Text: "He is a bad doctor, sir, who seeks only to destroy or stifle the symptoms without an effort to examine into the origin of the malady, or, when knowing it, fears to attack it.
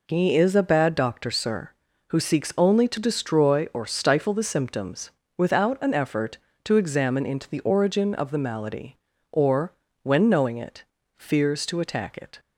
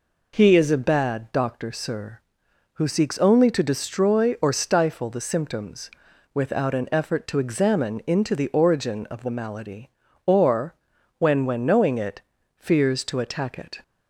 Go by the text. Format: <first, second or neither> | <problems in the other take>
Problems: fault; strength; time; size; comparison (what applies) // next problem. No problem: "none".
first | pauses between "symptoms" and "without"; at 5.9 s; 0.42 s long; slight in the first // says "when" twice; at 11.4 s